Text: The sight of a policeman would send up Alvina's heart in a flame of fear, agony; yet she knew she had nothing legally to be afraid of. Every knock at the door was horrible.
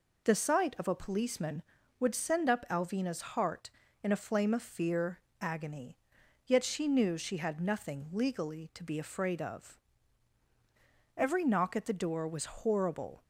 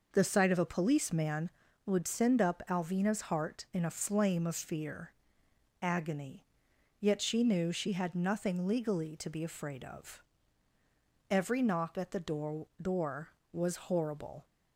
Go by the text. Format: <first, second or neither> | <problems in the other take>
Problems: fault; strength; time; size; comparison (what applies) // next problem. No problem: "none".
first | says "door" twice; at 12.8 s